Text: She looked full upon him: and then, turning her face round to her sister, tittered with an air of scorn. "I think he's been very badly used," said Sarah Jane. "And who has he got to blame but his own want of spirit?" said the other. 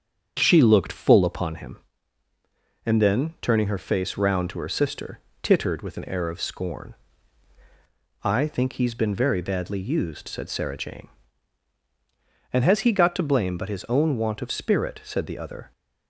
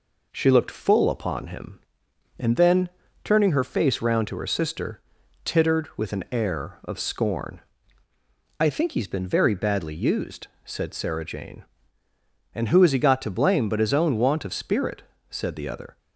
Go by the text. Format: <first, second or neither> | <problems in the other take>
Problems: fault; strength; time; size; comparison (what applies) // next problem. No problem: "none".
second | starts louder than the rest; strong; until 1.3 s; 7.5 dB // skips "who"; at 12.6 s